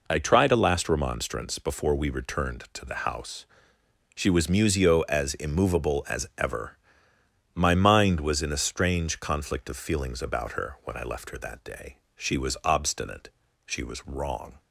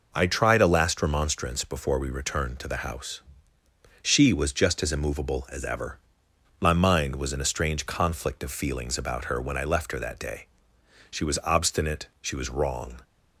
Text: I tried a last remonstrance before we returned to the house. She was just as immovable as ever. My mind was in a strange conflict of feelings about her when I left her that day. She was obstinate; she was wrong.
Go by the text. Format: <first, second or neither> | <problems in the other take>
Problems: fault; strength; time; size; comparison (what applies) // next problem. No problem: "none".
second | says "musio" for "just"; at 4.4 s